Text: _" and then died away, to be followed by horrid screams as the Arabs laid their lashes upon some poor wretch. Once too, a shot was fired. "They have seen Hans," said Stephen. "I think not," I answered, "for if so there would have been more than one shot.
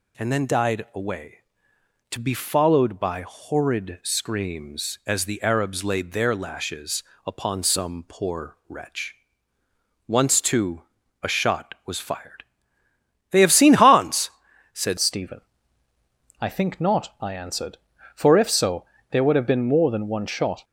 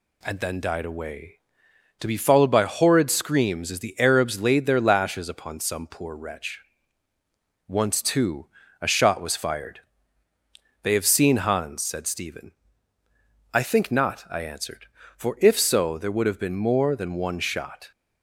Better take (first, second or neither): second